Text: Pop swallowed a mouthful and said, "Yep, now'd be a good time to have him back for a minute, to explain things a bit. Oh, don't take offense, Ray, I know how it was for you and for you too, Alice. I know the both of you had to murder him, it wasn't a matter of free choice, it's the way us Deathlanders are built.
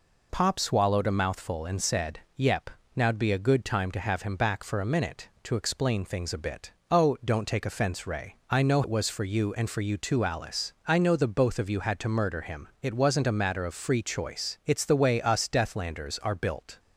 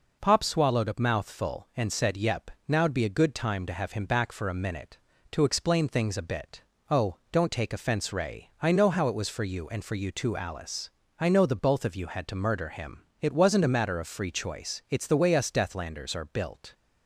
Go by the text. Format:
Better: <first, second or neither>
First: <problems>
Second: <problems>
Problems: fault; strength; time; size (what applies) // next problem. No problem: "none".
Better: second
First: skips "how"; at 8.8 s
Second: none